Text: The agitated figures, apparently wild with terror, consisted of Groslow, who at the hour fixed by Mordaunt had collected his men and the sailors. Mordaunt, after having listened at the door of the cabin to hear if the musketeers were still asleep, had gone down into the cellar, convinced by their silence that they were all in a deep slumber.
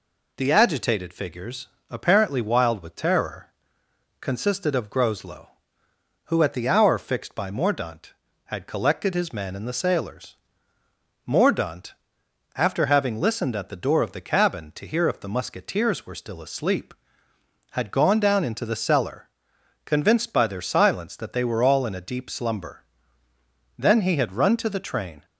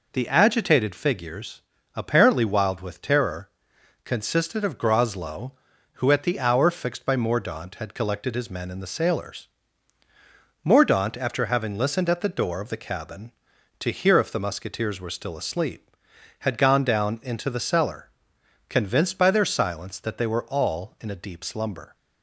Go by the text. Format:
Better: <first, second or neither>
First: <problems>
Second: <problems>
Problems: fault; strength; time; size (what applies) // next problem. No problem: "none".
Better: second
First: goes on to say "Then he had run to the train"; from 23.7 s on; 1.4 s long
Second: none